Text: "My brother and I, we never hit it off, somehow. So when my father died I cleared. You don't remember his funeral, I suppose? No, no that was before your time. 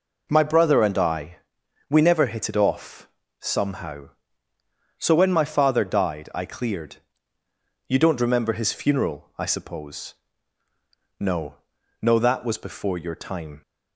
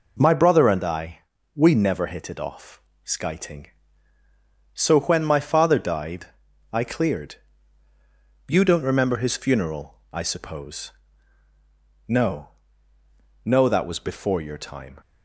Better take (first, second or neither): first